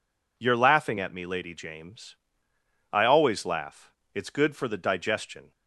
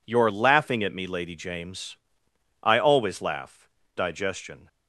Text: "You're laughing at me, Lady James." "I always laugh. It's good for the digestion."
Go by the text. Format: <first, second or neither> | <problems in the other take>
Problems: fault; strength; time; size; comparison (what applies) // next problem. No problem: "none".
first | skips "It's good for the"; at 3.8 s